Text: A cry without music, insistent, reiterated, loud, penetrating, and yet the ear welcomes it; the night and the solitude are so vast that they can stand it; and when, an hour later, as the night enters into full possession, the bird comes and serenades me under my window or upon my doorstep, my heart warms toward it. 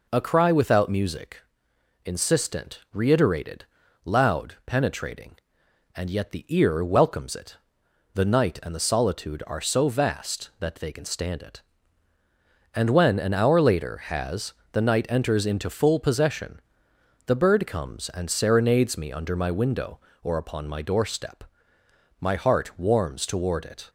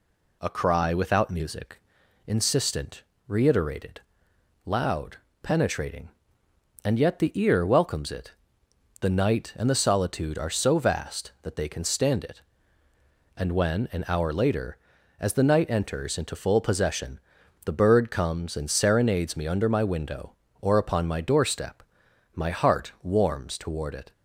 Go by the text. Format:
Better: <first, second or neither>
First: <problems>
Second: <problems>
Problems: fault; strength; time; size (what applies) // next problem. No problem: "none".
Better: second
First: says "has" for "as"; at 14.0 s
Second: none